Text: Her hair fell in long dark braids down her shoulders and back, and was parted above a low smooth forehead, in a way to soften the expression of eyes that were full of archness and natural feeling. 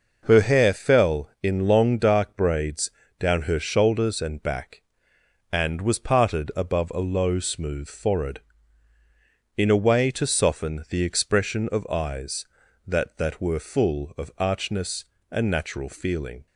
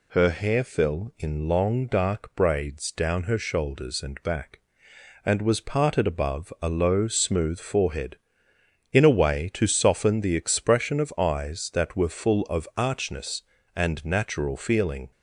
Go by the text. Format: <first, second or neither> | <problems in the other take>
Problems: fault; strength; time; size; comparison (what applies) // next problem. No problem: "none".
second | pauses between "braids" and "down"; slight; at 2.8 s; 0.30 s long // says "that" twice; at 13.1 s